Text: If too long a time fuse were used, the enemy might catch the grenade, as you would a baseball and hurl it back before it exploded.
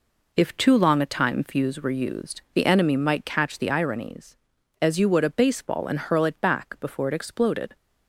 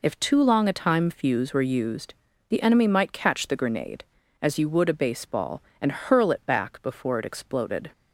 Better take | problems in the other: second | says "ironies" for "grenade"; at 3.7 s

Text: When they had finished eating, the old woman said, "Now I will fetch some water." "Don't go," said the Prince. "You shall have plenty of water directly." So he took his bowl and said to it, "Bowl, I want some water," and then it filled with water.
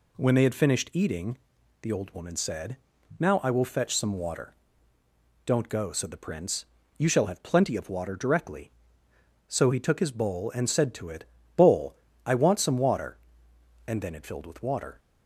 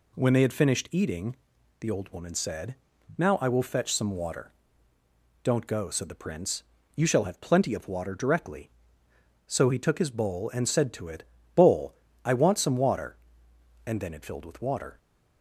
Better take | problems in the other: neither | none

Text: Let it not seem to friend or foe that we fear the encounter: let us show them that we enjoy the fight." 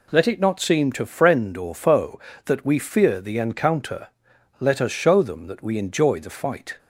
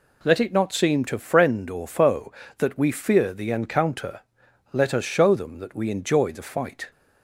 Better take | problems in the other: neither | none

